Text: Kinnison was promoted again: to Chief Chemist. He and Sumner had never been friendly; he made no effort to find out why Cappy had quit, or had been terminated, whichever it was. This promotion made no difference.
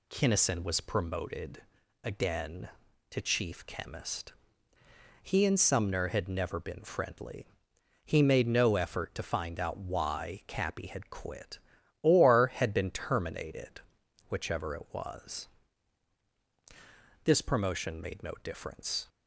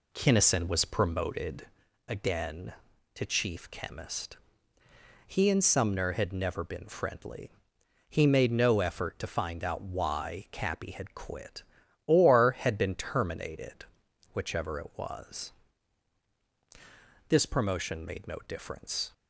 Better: first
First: pauses between "promoted" and "again"; at 1.6 s; 0.40 s long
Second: starts louder than the rest; slight; until 1.9 s; 2.5 dB // pauses between "promoted" and "again"; at 1.6 s; 0.40 s long

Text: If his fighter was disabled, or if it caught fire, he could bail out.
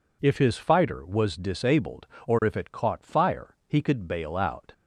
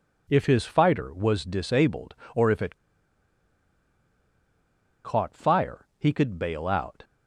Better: first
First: none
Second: pauses between "it" and "caught"; strong; at 2.7 s; 2.2 s long

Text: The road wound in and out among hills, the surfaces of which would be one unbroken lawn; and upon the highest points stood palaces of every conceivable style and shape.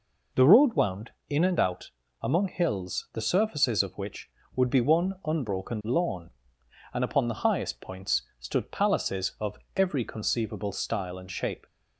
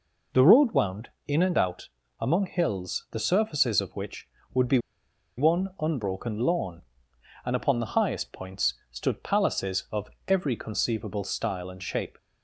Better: first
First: pauses between "out" and "among"; slight; at 1.9 s; 0.32 s long // pauses between "points" and "stood"; slight; at 8.2 s; 0.16 s long // pauses between "of" and "every"; slight; at 9.5 s; 0.20 s long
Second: pauses between "out" and "among"; slight; at 1.8 s; 0.32 s long // pauses between "be" and "one"; noticeable; at 4.7 s; 0.59 s long // pauses between "points" and "stood"; slight; at 8.7 s; 0.16 s long // pauses between "of" and "every"; slight; at 10.0 s; 0.20 s long

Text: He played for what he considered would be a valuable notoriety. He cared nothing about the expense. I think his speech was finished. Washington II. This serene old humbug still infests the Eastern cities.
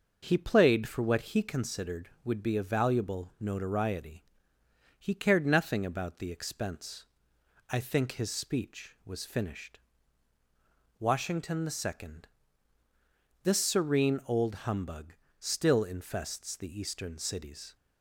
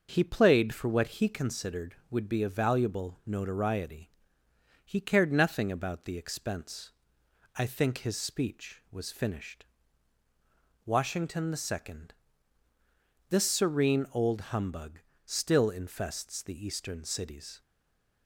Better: first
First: pauses between "humbug" and "still"; slight; at 15.1 s; 0.28 s long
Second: pauses between "humbug" and "still"; slight; at 14.9 s; 0.28 s long // stays silent after the last word; slight; from 17.6 s on; 0.6 s long

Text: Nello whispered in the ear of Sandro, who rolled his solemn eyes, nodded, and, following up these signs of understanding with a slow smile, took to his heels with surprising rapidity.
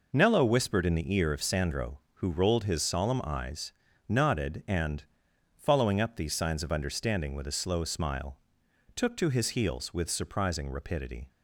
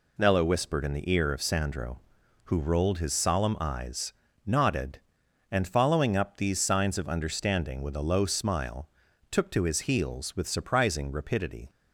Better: first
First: none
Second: says "low" for "slow"; at 8.0 s

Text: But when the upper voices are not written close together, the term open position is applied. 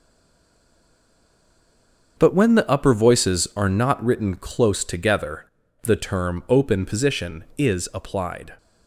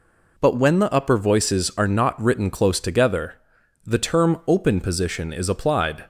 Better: second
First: stays silent before the first word; until 2.1 s; 2.1 s long // starts louder than the rest; until 3.1 s; 7 dB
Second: none

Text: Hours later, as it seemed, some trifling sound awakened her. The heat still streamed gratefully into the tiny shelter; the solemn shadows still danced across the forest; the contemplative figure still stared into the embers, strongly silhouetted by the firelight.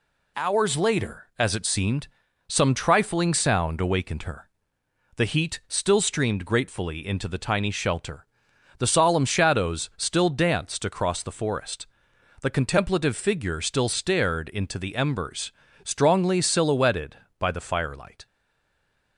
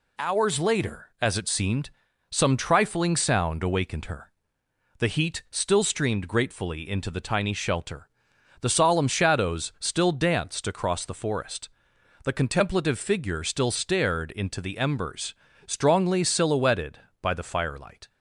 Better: second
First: stays silent after the last word; slight; from 18.2 s on; 0.9 s long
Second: none

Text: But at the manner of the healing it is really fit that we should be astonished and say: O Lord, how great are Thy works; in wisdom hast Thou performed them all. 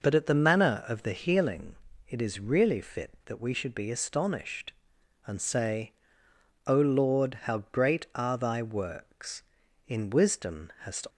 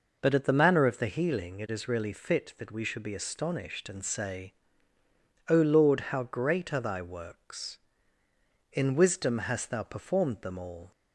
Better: second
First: pauses between "healing" and "it"; slight; at 1.7 s; 0.32 s long // stops before "Thou performed them all"; at 11.0 s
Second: none

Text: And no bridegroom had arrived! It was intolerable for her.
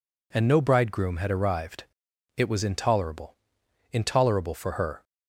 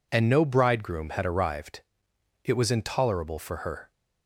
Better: second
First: says "intolerable" twice; at 3.9 s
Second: none

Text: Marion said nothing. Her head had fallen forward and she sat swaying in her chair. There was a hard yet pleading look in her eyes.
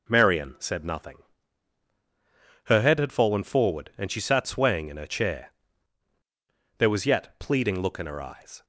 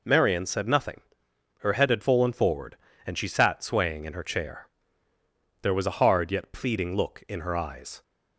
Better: second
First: skips "a hard"; at 7.0 s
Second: none

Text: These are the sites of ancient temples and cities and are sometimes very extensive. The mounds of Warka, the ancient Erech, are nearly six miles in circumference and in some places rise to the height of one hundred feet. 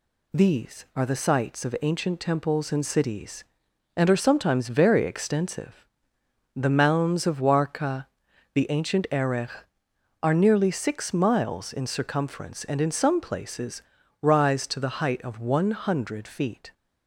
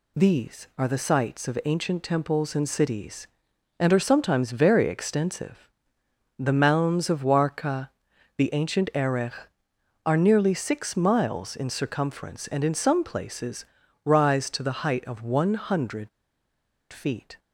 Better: first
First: pauses between "places" and "rise"; at 13.8 s; 0.40 s long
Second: pauses between "places" and "rise"; at 13.6 s; 0.40 s long // pauses between "hundred" and "feet"; noticeable; at 16.0 s; 0.83 s long

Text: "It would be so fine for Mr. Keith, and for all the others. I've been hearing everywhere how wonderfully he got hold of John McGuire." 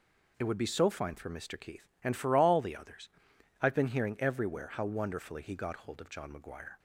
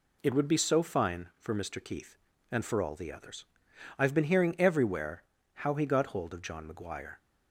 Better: first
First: none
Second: pauses between "everywhere" and "how"; slight; at 5.2 s; 0.32 s long // skips "wonderfully"; at 5.7 s

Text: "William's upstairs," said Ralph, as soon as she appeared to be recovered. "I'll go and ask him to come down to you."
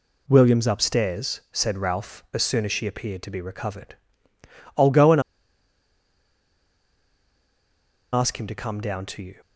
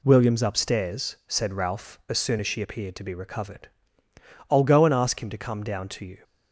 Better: second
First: pauses between "and" and "ask"; strong; at 5.2 s; 2.9 s long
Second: none

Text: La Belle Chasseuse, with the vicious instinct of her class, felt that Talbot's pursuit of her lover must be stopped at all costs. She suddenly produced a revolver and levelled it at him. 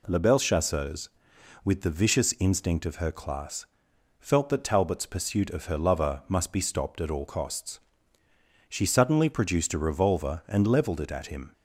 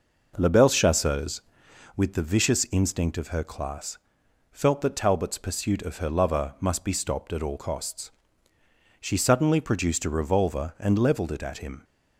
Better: first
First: none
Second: starts louder than the rest; noticeable; until 1.8 s; 5.5 dB

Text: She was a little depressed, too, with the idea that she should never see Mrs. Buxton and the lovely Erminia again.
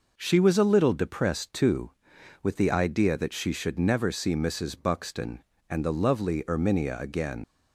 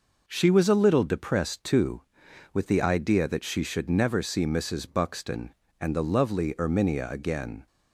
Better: second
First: leaves "again" unfinished; at 7.4 s; 115 ms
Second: none

